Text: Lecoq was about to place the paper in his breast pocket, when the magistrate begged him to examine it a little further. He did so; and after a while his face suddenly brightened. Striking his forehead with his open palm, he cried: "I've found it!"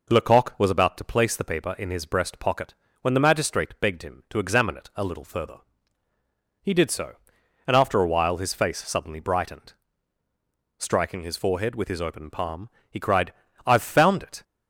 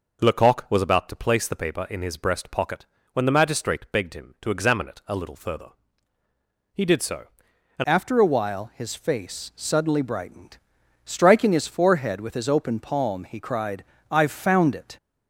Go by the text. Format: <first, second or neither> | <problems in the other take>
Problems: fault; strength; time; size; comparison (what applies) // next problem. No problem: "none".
first | changes voice at "after"; from 7.8 s on; 7.1 s long